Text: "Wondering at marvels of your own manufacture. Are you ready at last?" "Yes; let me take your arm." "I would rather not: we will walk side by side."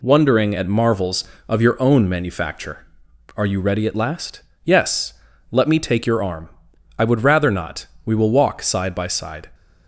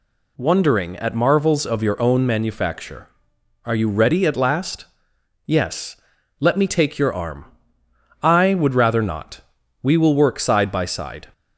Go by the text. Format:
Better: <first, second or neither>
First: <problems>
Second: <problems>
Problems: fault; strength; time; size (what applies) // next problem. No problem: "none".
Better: first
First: none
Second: says "work" for "walk"; at 10.1 s